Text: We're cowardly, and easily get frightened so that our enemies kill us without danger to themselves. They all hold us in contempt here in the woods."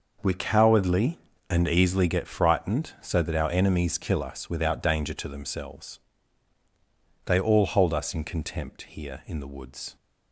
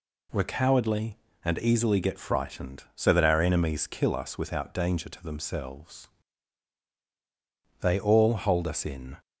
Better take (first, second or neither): first